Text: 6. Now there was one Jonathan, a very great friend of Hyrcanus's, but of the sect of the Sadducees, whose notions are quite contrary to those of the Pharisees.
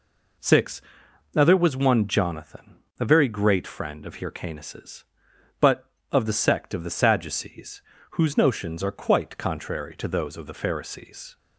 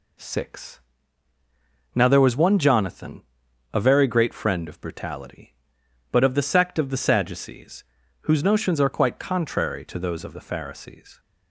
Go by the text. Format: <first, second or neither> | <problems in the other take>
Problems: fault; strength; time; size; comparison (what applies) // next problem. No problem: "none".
first | says "Brutality" for "Hyrcanus's"; at 4.8 s